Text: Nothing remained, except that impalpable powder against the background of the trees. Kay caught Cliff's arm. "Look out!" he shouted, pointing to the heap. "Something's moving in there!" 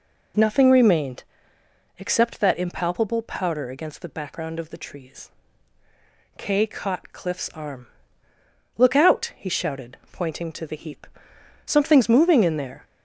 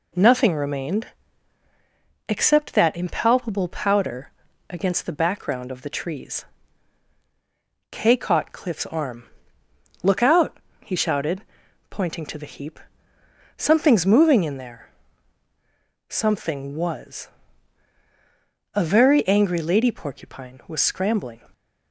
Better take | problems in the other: first | pauses between "powder" and "against"; at 4.3 s; 0.38 s long // goes on to say "Something was A very angry lady porcupine was scrambling"; strong; from 16.1 s on; 5.3 s long

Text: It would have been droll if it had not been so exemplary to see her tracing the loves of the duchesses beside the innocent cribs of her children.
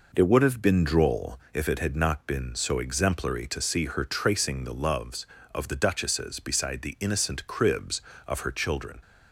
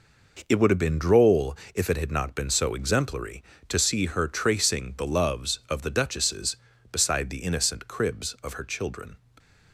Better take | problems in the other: neither | pauses between "droll" and "if"; slight; the same in both

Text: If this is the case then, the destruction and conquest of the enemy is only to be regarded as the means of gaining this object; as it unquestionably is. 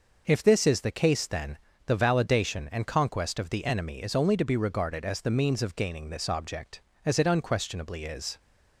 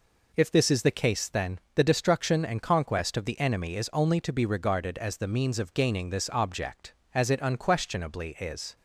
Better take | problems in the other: second | says "validation" for "destruction"; at 1.9 s

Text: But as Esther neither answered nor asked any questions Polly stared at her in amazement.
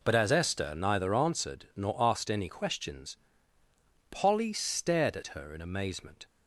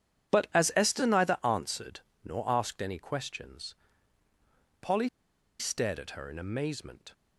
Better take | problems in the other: first | pauses between "answered" and "nor"; slight; at 2.0 s; 0.22 s long // pauses between "questions" and "Polly"; at 3.7 s; 1.0 s long; noticeable in the first // pauses between "Polly" and "stared"; noticeable; at 5.0 s; 0.51 s long

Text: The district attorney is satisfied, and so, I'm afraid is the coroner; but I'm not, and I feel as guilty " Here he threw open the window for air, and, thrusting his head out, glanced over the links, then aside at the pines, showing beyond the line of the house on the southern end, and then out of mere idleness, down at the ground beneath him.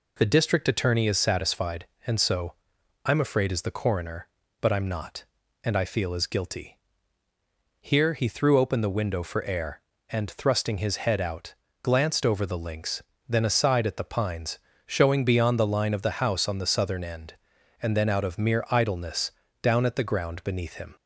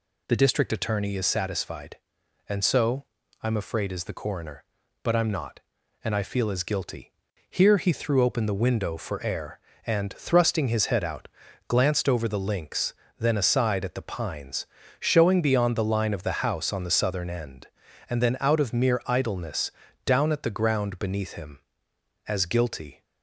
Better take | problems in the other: first | goes on to say "As guilty"; noticeable; from 22.2 s on; 0.76 s long

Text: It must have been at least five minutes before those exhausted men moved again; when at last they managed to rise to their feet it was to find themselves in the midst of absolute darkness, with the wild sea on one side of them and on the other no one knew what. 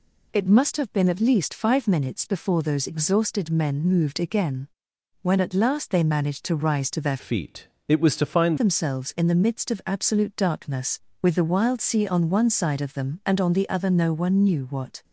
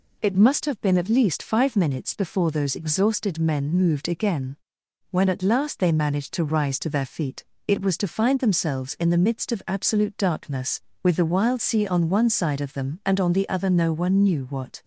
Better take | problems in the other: second | changes voice from "feet" to "find"; from 7.1 to 8.5 s; 1.4 s long // pauses between "feet" and "it"; slight; at 7.6 s; 0.22 s long; slight in the second

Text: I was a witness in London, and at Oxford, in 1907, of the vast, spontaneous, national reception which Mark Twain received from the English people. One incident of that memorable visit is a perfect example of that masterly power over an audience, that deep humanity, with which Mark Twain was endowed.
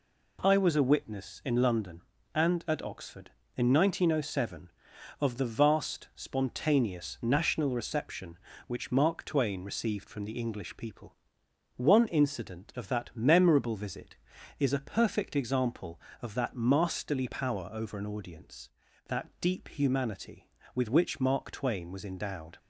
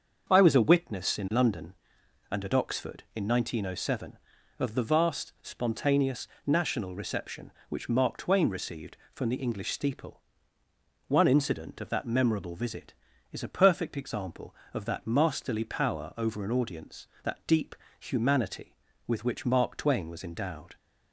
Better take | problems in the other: first | starts louder than the rest; until 1.2 s; 6.5 dB // says "steeple" for "people"; at 9.7 s // pauses between "deep" and "humanity"; slight; at 17.7 s; 0.24 s long

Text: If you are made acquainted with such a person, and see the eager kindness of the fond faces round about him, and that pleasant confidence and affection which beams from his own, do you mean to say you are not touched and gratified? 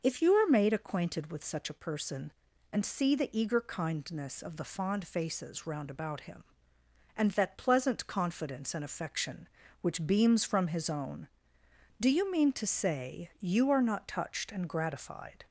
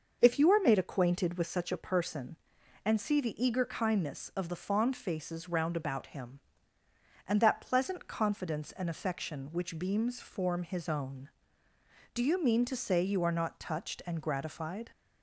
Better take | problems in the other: first | says "form" for "from"; at 10.2 s

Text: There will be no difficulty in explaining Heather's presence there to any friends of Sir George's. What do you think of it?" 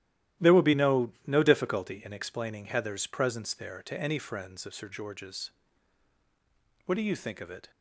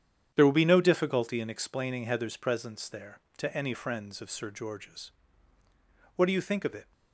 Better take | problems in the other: second | starts louder than the rest; strong; until 1.5 s; 13 dB; strong in the second // says "no" twice; at 1.2 s

